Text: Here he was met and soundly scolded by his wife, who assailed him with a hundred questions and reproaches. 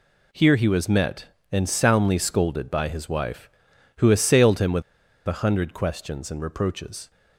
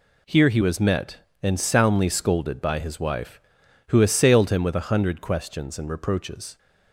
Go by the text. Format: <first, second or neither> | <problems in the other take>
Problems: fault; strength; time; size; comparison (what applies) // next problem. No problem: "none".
second | pauses between "with" and "a"; at 4.8 s; 0.45 s long